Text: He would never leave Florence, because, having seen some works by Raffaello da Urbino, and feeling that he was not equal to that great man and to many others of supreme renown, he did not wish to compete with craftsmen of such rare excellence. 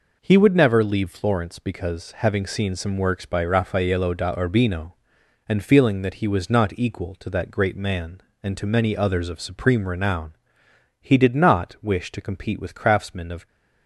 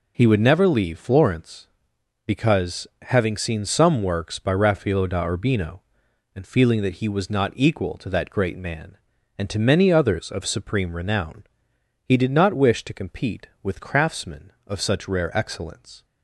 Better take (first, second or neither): second